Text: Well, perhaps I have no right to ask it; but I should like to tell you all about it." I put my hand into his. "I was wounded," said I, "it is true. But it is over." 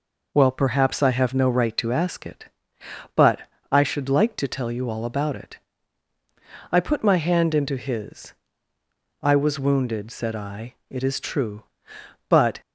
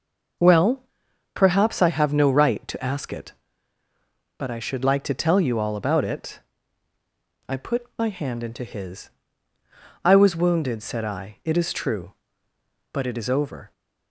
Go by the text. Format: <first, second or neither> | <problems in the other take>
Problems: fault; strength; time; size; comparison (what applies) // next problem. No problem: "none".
second | pauses between "but" and "I"; slight; at 3.4 s; 0.30 s long // stops before "it is over"; at 12.6 s